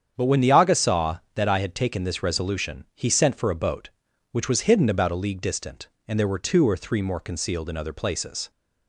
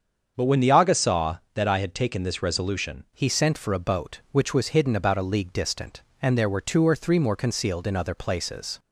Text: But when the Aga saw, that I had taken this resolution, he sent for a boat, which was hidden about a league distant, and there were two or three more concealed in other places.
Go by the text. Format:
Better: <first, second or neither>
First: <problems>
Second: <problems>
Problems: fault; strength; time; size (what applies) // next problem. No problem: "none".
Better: first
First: starts louder than the rest; strong; until 1.1 s; 8 dB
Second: starts louder than the rest; strong; until 1.3 s; 7 dB // changes voice at "he"; from 3.1 s on; 5.6 s long